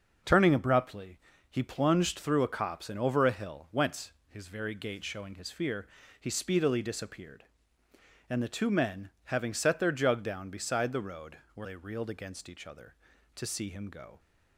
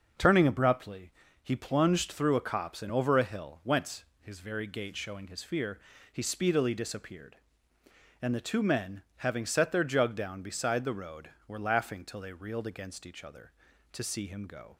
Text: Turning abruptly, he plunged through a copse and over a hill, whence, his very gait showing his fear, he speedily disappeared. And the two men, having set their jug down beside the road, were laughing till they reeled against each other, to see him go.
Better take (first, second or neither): second